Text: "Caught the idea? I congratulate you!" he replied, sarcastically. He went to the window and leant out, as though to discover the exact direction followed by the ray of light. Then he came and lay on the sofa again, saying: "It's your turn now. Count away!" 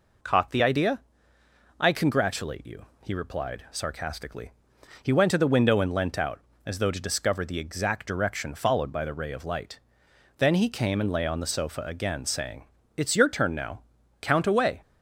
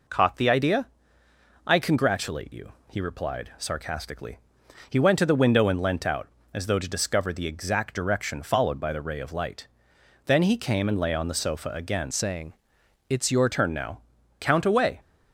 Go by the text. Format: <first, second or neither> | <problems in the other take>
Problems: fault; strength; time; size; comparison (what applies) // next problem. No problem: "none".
first | changes voice from "saying" to "your"; from 12.1 to 13.4 s; 1.3 s long